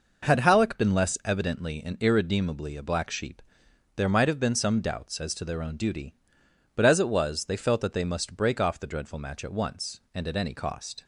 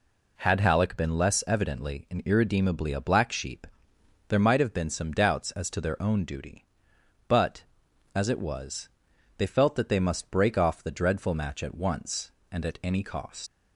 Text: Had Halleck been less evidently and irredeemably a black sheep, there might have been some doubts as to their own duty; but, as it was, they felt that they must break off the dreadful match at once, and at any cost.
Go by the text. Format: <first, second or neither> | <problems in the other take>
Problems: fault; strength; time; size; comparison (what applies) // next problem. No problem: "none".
first | leaves "cost" unfinished; at 13.4 s; 105 ms